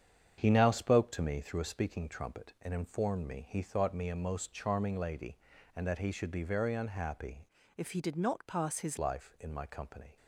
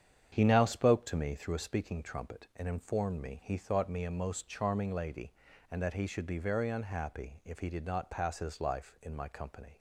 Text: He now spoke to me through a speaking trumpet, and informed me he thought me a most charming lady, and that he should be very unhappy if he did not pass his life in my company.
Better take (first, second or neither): second